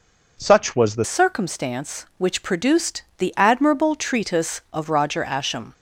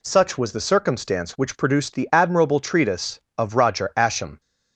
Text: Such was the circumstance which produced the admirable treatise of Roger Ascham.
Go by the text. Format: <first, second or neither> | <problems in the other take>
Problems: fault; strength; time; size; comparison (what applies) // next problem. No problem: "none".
second | changes voice at "circumstance"; from 1.0 s on; 4.7 s long // pauses between "produced" and "the"; slight; at 3.0 s; 0.16 s long